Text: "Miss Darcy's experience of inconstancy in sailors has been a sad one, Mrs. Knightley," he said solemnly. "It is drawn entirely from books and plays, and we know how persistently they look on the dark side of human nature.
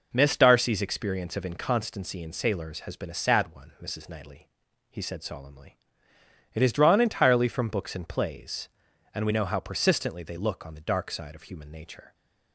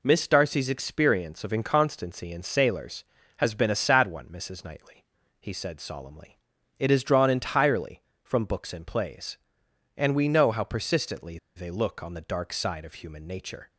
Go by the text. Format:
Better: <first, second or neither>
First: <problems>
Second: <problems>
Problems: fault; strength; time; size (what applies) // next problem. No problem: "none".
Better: first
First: none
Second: pauses between "persistently" and "they"; slight; at 11.3 s; 0.19 s long